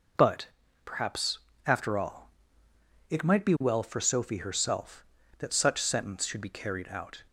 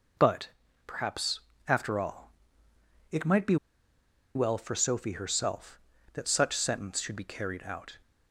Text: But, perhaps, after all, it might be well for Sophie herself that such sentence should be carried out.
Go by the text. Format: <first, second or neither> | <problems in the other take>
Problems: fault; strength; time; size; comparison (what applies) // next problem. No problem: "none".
first | pauses between "be" and "well"; noticeable; at 3.5 s; 0.79 s long